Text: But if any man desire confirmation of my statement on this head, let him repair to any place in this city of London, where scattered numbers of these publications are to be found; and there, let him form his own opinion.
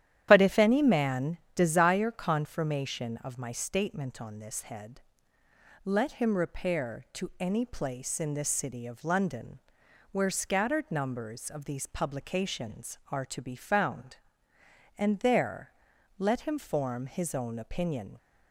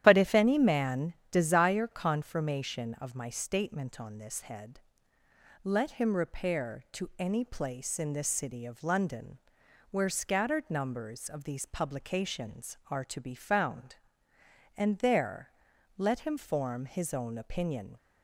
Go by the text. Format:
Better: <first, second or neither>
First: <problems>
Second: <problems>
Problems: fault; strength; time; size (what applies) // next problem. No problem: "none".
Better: neither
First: starts louder than the rest; strong; until 1.3 s; 11 dB // pauses between "man" and "desire"; slight; at 1.3 s; 0.18 s long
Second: starts louder than the rest; strong; until 1.0 s; 11 dB // pauses between "man" and "desire"; slight; at 1.1 s; 0.18 s long